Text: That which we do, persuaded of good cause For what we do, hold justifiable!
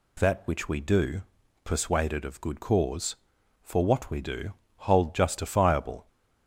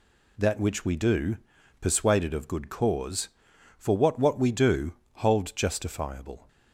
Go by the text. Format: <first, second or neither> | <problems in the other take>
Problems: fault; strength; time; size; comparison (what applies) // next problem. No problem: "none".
first | says "what" twice; at 4.1 s